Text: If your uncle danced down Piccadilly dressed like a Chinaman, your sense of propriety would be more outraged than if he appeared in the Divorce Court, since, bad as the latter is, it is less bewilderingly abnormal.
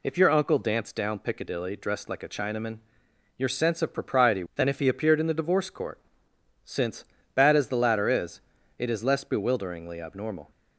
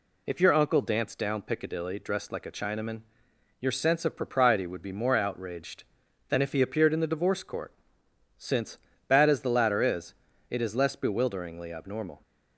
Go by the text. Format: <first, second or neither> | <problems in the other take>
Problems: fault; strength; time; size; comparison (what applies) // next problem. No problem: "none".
second | skips "would be more outraged"; at 4.5 s